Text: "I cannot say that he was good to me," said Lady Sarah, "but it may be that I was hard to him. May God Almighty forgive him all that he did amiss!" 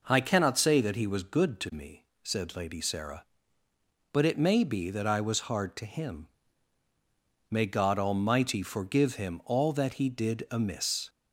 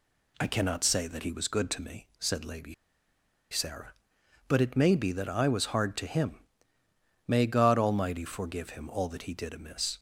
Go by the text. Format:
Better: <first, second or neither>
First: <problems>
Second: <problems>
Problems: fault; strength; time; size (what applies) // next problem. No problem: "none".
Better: first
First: none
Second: pauses between "Lady" and "Sarah"; noticeable; at 2.7 s; 0.77 s long